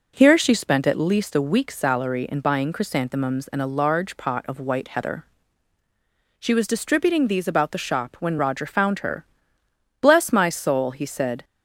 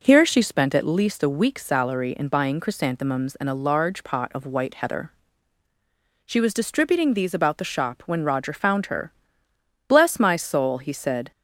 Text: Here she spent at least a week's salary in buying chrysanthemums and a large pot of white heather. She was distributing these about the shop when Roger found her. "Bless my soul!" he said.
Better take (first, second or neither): neither